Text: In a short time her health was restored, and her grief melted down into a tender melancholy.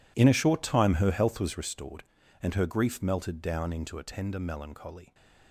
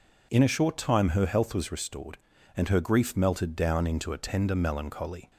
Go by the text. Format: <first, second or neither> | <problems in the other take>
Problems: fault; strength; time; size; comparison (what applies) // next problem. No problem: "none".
second | gets quieter; strong; throughout; 17 dB